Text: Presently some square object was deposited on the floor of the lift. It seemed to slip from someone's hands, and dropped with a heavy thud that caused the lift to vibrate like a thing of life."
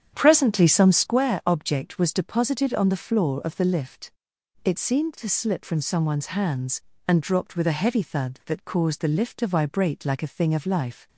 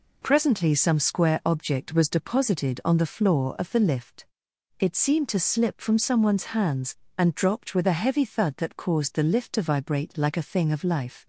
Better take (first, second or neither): second